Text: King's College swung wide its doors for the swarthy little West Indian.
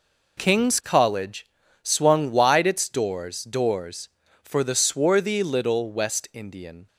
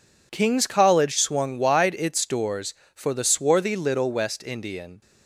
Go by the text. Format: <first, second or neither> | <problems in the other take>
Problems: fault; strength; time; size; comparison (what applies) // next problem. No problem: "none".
second | pauses between "College" and "swung"; at 1.4 s; 0.38 s long // says "doors" twice; at 3.4 s